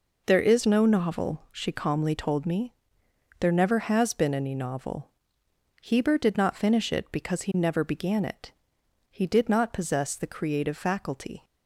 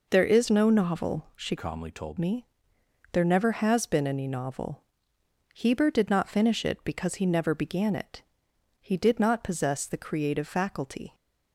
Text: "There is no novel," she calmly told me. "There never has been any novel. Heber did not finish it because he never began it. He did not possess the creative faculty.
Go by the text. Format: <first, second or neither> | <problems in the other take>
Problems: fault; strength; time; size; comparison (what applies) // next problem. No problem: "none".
first | changes voice from "calmly" to "told"; from 1.5 to 2.1 s; 0.6 s long